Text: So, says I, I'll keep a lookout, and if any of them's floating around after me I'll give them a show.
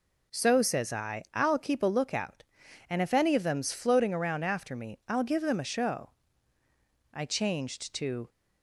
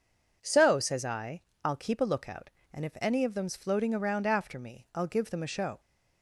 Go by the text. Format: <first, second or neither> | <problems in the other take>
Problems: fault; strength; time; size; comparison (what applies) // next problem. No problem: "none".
second | goes on to say "I changed to"; noticeable; from 7.1 s on; 1.1 s long